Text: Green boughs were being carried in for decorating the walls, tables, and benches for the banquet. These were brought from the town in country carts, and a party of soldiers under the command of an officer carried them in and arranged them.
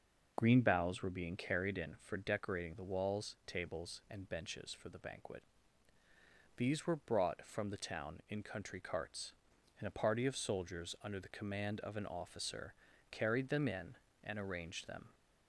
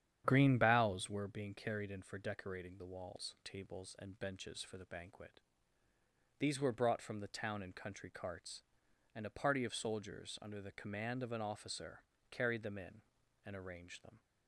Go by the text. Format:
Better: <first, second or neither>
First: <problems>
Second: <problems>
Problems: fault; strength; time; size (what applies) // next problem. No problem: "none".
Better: first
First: pauses between "officer" and "carried"; slight; at 12.7 s; 0.36 s long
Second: starts louder than the rest; strong; until 1.4 s; 9.5 dB // pauses between "officer" and "carried"; slight; at 12.0 s; 0.30 s long